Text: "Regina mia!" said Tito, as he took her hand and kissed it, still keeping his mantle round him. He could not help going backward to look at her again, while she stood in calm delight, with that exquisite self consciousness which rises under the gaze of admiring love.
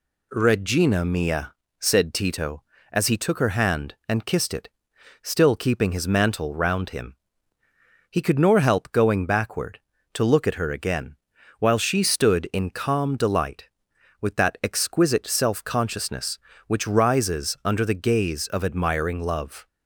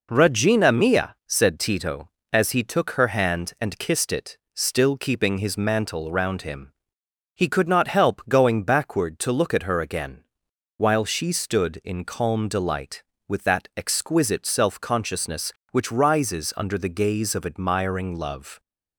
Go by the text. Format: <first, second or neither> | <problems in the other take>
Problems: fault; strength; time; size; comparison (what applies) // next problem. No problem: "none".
second | says "nor" for "not"; at 8.3 s